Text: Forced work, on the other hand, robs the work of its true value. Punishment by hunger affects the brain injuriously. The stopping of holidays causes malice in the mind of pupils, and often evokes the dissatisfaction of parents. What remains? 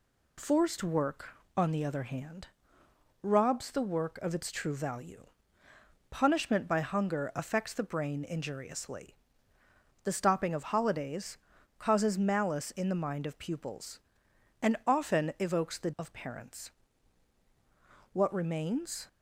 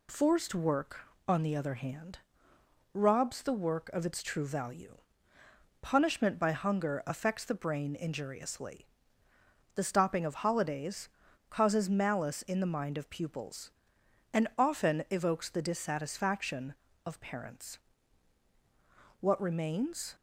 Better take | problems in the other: second | pauses between "holidays" and "causes"; at 11.3 s; 0.38 s long; also in the second // skips "dissatisfaction"; at 15.9 s

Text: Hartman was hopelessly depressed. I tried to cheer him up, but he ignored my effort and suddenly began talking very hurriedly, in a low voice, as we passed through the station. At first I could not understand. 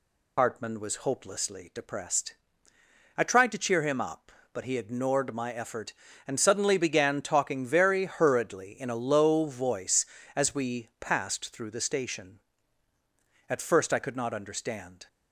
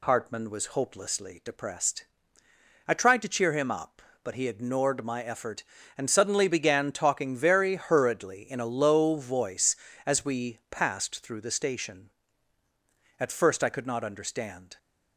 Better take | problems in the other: second | loses the start of "Hartman"; at 0.3 s; 55 ms

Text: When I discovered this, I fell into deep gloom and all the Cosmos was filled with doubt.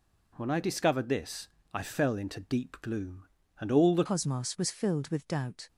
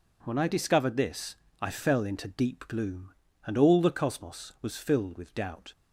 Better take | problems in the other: second | changes voice at "Cosmos"; from 4.0 s on; 1.6 s long

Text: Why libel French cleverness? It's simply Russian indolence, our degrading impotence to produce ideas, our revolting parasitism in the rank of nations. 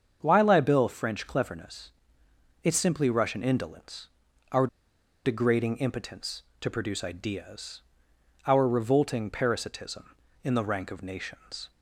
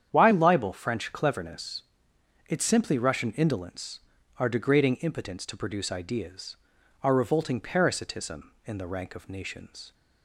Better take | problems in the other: second | starts louder than the rest; strong; until 1.2 s; 7 dB; strong in the second // pauses between "our" and "degrading"; noticeable; at 4.6 s; 0.58 s long

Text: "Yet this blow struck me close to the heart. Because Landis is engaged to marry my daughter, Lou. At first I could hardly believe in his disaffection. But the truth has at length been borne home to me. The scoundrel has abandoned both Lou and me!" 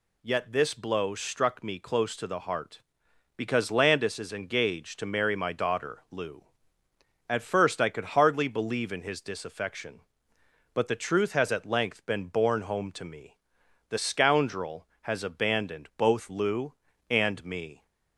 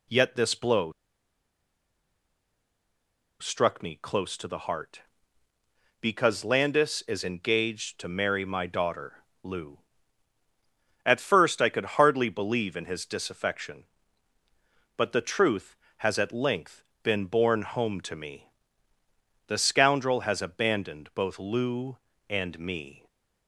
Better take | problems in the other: first | pauses between "blow" and "struck"; strong; at 0.9 s; 2.4 s long // pauses between "length" and "been"; slight; at 16.8 s; 0.20 s long

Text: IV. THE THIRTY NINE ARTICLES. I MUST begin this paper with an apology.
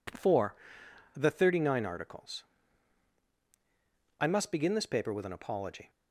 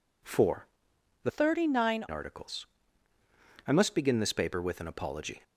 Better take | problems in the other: first | changes voice from "THIRTY" to "NINE"; from 1.2 to 2.0 s; 0.8 s long

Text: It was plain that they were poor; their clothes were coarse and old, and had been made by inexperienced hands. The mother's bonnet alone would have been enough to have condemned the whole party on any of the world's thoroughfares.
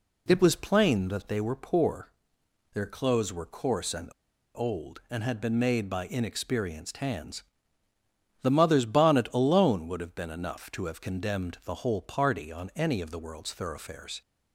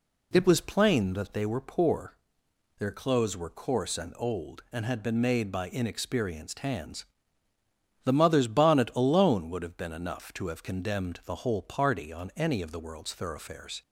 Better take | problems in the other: second | pauses between "and" and "old"; at 4.0 s; 0.45 s long

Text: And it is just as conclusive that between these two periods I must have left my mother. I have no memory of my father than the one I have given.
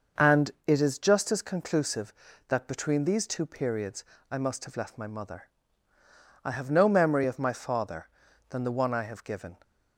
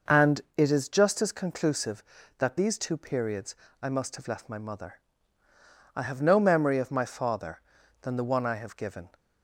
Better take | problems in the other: first | pauses between "And" and "it"; slight; at 0.4 s; 0.16 s long; slight in the first // skips "between"; at 2.5 s // pauses between "periods" and "I"; slight; at 3.5 s; 0.28 s long; slight in the first

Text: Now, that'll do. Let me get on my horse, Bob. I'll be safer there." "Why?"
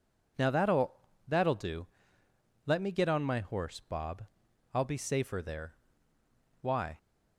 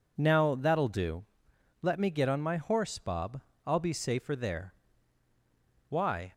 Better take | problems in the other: second | says "that'll" twice; at 1.2 s

